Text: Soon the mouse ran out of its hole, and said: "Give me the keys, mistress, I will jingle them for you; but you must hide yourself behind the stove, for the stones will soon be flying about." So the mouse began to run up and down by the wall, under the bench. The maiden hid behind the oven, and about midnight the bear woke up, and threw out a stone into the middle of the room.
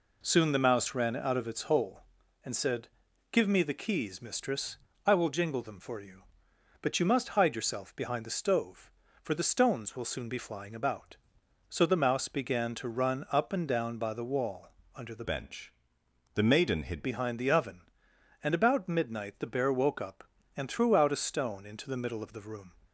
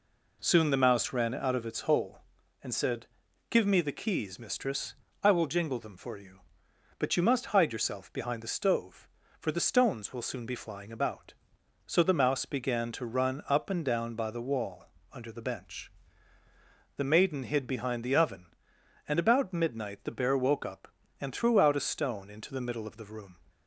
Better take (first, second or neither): second